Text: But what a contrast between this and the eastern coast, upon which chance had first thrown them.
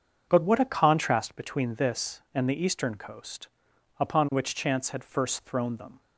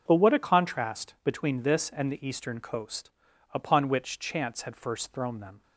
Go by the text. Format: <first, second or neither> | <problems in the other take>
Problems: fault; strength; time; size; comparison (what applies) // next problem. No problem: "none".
neither | starts louder than the rest; the same in both